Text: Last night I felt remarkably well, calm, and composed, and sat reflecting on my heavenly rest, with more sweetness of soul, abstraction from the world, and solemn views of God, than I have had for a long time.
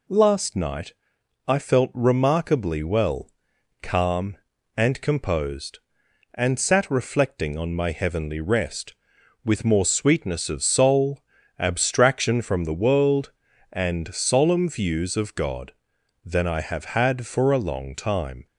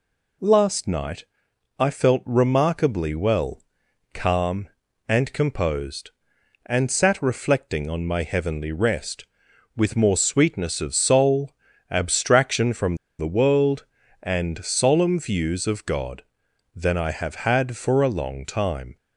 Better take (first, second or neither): first